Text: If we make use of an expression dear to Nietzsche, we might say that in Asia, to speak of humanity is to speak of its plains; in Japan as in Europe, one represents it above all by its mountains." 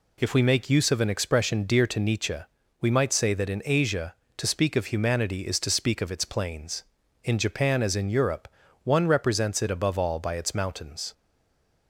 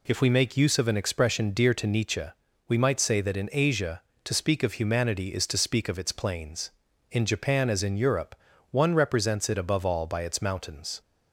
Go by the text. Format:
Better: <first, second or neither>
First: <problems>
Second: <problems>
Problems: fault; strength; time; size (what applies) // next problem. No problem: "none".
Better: second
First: stays silent after the last word; slight; from 11.1 s on; 0.7 s long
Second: none